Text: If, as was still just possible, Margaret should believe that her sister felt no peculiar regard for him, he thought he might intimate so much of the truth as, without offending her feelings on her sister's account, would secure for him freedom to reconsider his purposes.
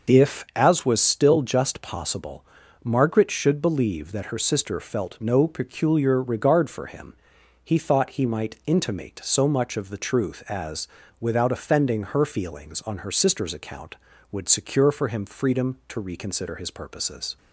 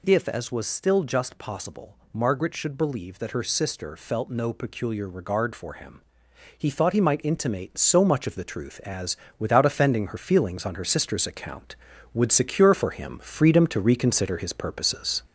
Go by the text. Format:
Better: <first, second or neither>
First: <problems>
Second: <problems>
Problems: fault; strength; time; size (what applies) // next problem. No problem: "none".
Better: first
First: none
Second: gets louder; noticeable; throughout; 4.5 dB